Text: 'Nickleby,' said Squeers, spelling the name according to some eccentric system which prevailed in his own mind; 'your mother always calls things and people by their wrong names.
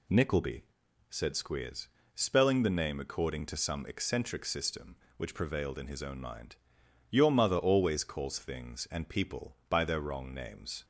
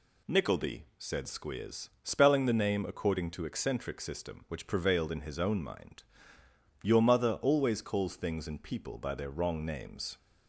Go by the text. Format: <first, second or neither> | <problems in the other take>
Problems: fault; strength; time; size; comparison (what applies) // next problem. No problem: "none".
first | skips "some"; at 3.4 s